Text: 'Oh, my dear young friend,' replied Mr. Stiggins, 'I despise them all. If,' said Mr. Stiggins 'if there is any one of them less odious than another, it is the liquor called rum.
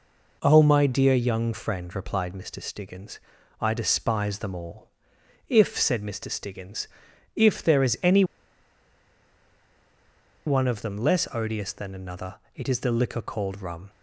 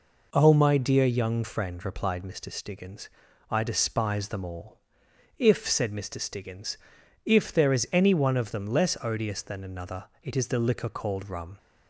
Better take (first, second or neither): second